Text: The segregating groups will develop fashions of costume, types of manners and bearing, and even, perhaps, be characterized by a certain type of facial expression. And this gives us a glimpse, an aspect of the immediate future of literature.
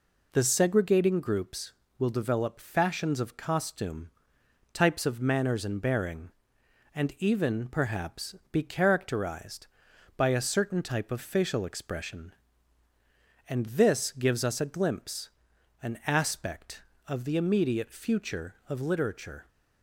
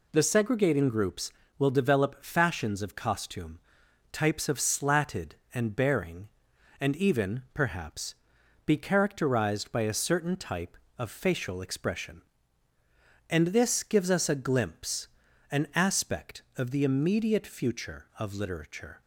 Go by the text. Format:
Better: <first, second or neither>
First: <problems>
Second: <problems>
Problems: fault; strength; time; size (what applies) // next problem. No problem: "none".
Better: first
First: none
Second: says "slatted" for "manners"; at 4.5 s